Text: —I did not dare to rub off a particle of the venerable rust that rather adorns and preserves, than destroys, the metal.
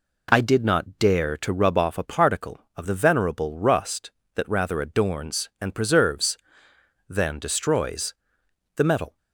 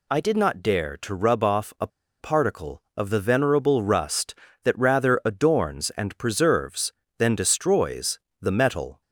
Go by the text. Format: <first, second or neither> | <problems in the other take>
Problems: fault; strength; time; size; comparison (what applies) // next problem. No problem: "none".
first | pauses between "a" and "particle"; slight; at 1.8 s; 0.32 s long